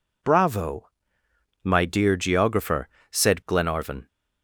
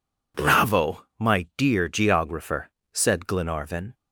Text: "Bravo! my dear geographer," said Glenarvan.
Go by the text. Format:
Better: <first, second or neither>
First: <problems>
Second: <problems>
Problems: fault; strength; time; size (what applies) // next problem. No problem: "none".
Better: neither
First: none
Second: none